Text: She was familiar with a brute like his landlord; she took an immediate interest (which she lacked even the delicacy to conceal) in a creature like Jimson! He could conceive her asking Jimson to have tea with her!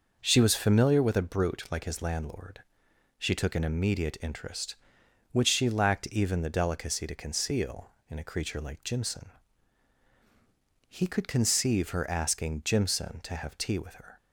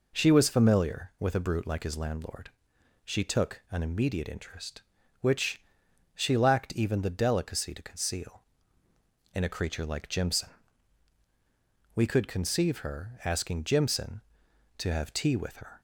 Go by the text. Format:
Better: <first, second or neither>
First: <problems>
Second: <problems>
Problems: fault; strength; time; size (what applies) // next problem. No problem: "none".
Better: first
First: none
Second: pauses between "which" and "she"; noticeable; at 5.5 s; 0.54 s long // says "We" for "He"; at 11.9 s